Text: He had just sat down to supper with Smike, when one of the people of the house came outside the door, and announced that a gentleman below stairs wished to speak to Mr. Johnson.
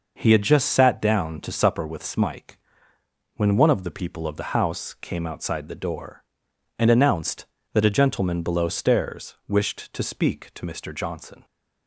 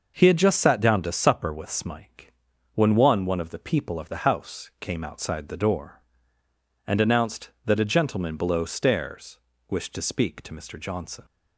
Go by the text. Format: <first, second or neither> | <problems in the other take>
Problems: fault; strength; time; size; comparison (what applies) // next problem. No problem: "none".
first | says "one" twice; at 3.2 s // pauses between "stairs" and "wished"; slight; at 9.3 s; 0.30 s long